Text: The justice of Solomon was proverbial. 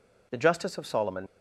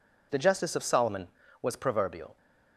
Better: second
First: stops before "was proverbial"; at 1.2 s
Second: none

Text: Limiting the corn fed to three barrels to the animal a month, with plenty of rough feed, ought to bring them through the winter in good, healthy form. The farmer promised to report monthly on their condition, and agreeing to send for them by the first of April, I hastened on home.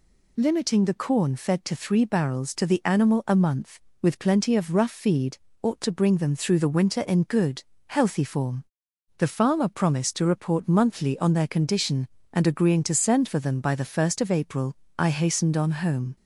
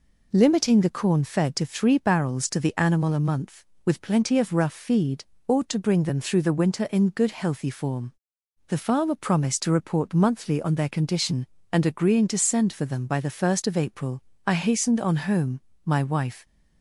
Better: first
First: none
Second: goes on to say "My wife"; noticeable; from 15.8 s on; 0.62 s long

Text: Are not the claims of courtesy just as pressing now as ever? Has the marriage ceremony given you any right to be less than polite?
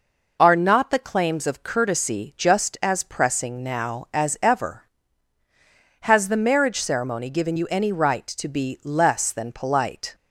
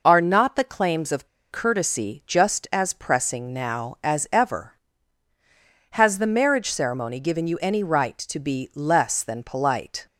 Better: first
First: none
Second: pauses between "of" and "courtesy"; slight; at 1.2 s; 0.24 s long

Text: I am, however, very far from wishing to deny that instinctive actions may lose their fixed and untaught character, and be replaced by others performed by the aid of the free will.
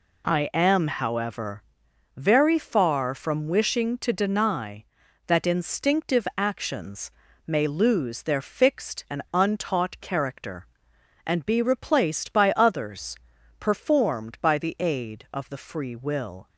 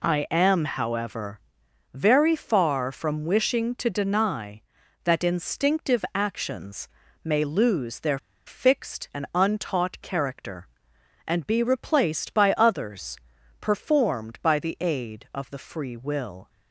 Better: first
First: pauses between "actions" and "may"; slight; at 7.1 s; 0.34 s long // pauses between "others" and "performed"; at 13.1 s; 0.44 s long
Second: pauses between "actions" and "may"; slight; at 6.8 s; 0.34 s long // pauses between "their" and "fixed"; slight; at 8.1 s; 0.27 s long // pauses between "others" and "performed"; at 13.1 s; 0.44 s long

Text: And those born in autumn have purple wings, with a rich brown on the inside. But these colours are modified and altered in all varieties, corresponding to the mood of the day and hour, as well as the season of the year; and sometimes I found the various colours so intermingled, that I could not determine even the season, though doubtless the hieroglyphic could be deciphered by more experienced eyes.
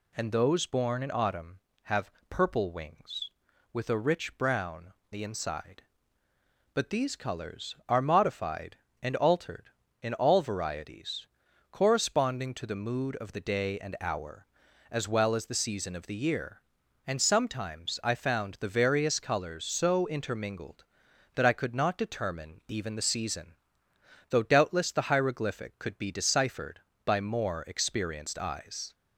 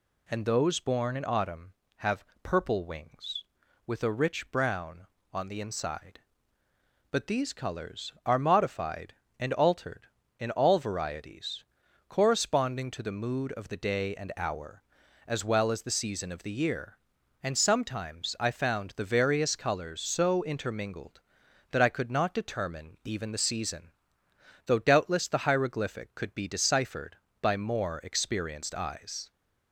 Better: second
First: pauses between "have" and "purple"; slight; at 2.1 s; 0.18 s long // skips "on"; at 5.0 s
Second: pauses between "have" and "purple"; slight; at 2.2 s; 0.18 s long

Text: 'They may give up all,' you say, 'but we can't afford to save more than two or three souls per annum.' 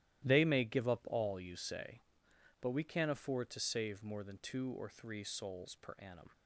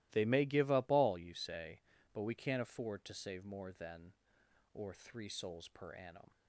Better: first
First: starts louder than the rest; strong; until 1.3 s; 13.5 dB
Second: starts louder than the rest; strong; until 1.1 s; 16.5 dB // skips "two"; at 4.4 s

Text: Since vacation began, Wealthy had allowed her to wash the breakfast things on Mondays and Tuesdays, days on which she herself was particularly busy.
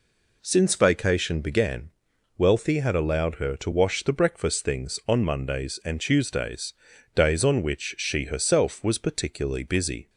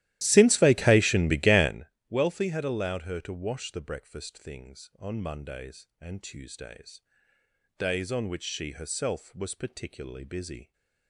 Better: first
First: none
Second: starts louder than the rest; strong; until 1.8 s; 14.5 dB

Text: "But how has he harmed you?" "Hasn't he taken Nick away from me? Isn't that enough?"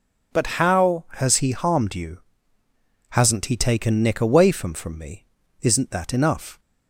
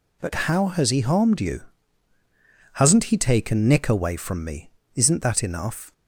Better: second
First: says "from" twice; at 4.7 s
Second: none

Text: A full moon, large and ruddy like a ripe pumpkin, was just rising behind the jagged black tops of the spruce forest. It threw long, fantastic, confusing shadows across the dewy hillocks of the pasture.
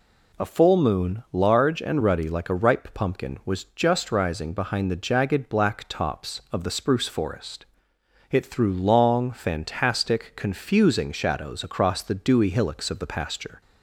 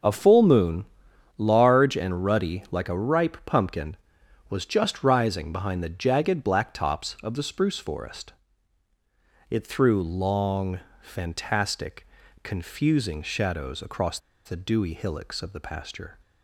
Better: first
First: none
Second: starts louder than the rest; until 1.5 s; 6 dB // pauses between "across" and "the"; slight; at 14.1 s; 0.27 s long

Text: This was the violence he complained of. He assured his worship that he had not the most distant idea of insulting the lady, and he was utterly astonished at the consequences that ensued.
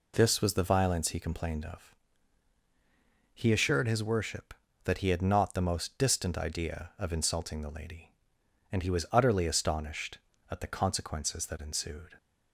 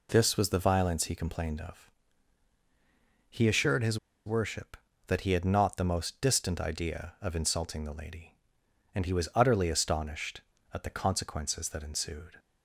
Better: first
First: none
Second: pauses between "his" and "worship"; slight; at 3.9 s; 0.29 s long

